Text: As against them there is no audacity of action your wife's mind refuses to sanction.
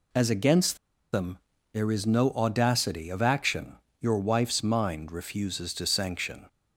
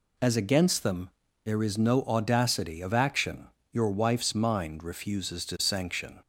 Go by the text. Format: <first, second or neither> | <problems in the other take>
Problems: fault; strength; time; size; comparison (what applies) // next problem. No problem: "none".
second | pauses between "against" and "them"; at 0.7 s; 0.37 s long // pauses between "them" and "there"; slight; at 1.3 s; 0.36 s long; slight in the second // pauses between "action" and "your"; slight; at 3.7 s; 0.22 s long; slight in the second